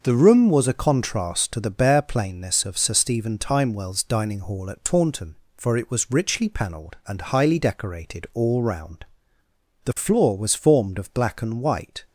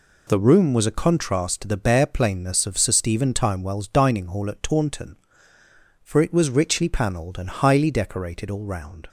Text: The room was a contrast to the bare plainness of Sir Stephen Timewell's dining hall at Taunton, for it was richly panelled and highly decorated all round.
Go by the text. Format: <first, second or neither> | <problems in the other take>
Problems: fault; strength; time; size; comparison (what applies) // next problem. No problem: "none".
second | starts louder than the rest; until 1.0 s; 6 dB // goes on to say "The floor was formed of black and white"; strong; from 9.8 s on; 2.1 s long